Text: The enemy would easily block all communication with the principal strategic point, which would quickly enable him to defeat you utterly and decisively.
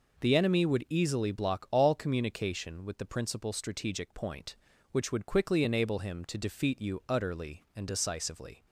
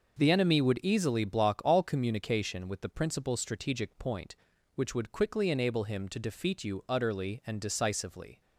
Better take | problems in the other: neither | none

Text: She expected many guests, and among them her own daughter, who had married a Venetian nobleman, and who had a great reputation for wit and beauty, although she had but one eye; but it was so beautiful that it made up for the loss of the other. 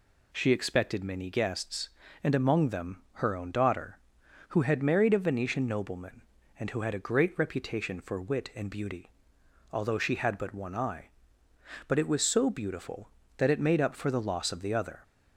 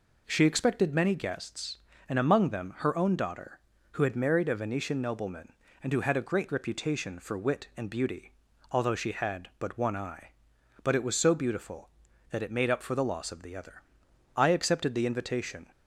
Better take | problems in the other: first | goes on to say "I accepted the invitation"; from 14.3 s on; 1.3 s long

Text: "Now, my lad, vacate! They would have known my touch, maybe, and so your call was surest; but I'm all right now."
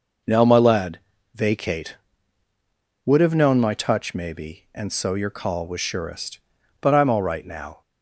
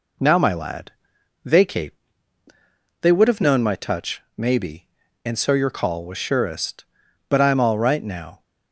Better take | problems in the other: second | skips "They"; at 2.5 s

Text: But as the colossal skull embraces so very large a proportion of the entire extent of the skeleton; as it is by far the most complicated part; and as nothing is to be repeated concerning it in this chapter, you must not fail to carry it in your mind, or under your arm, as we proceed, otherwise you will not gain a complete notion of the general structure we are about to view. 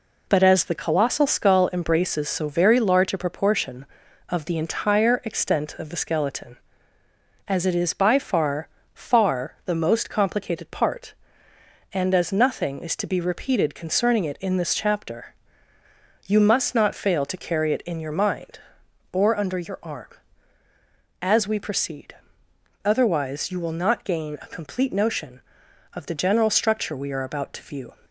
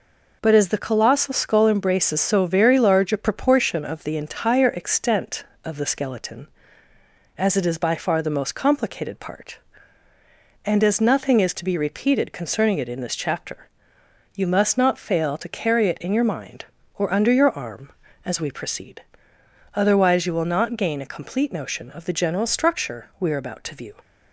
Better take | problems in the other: second | says "far" twice; at 8.9 s

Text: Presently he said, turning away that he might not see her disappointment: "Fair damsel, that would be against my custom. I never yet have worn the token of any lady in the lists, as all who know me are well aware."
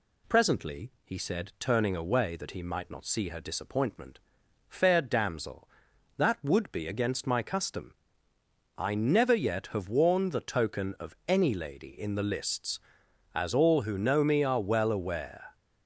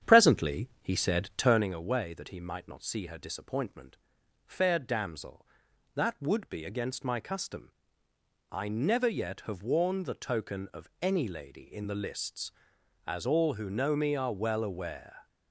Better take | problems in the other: first | starts louder than the rest; strong; until 1.7 s; 9 dB

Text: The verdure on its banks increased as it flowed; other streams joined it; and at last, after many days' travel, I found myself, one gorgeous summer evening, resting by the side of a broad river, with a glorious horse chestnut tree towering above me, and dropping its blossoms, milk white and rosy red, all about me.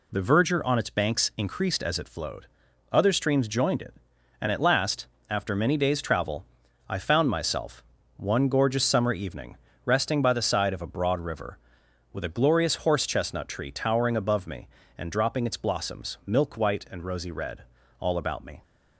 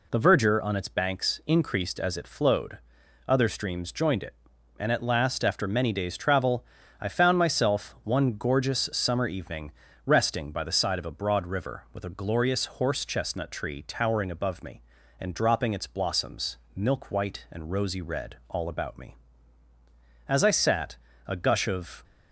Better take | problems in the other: first | pauses between "glorious" and "horse"; slight; at 12.6 s; 0.16 s long // goes on to say "As I sat a gush of"; strong; from 20.2 s on; 1.7 s long

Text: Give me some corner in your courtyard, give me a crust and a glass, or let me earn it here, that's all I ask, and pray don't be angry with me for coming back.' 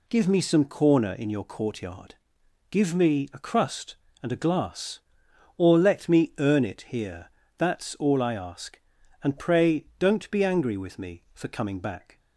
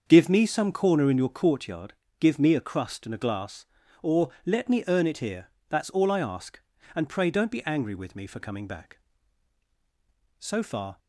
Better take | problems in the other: first | starts louder than the rest; until 1.0 s; 7 dB // pauses between "or" and "let"; slight; at 4.2 s; 0.16 s long // goes on to say "So far"; from 10.3 s on; 0.60 s long

